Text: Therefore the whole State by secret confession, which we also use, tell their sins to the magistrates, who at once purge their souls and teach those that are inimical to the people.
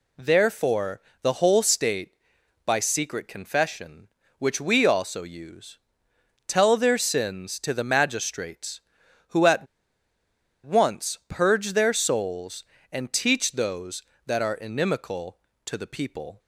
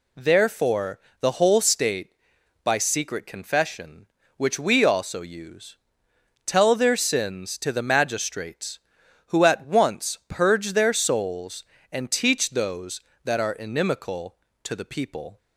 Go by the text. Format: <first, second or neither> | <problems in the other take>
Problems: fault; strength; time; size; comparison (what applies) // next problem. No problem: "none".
second | pauses between "Therefore" and "the"; slight; at 1.0 s; 0.20 s long; slight in the second // pauses between "at" and "once"; at 9.6 s; 0.98 s long